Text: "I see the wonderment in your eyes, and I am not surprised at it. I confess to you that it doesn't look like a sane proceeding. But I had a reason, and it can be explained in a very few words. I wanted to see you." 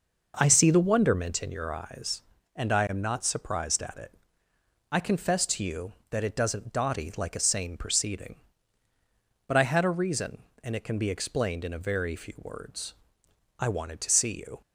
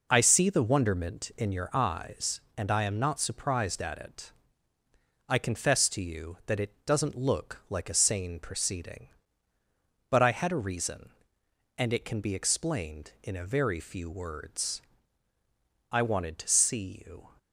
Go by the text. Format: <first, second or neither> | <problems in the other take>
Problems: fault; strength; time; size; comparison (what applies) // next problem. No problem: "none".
second | says "dotty" for "look"; at 6.7 s